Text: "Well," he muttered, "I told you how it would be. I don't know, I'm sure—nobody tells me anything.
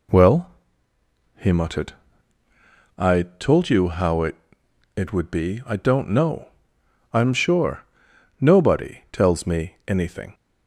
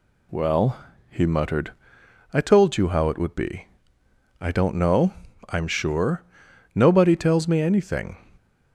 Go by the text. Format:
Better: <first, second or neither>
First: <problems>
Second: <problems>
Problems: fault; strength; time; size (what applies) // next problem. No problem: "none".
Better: second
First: says "it" twice; at 4.9 s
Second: none